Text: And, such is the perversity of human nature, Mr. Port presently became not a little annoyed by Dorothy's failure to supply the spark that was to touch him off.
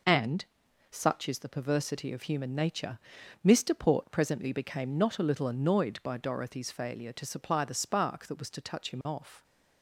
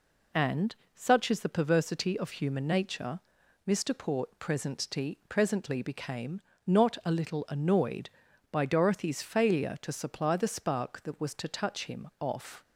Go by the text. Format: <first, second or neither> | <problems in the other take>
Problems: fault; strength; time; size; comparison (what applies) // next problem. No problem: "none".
first | says "presently" twice; at 5.2 s // pauses between "became" and "not"; slight; at 6.3 s; 0.26 s long